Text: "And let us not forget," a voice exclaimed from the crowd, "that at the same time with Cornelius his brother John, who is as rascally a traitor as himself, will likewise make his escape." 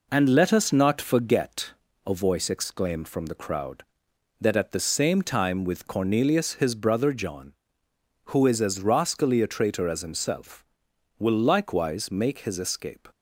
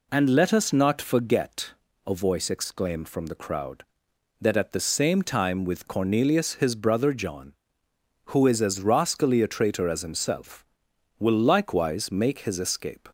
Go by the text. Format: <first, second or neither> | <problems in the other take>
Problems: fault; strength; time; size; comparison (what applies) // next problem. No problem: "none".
second | gets quieter; noticeable; throughout; 4 dB